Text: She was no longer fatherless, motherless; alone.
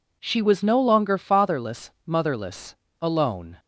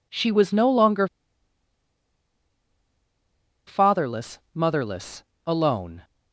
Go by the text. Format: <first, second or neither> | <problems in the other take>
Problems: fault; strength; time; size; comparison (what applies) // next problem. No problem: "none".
first | pauses between "longer" and "fatherless"; strong; at 1.0 s; 2.6 s long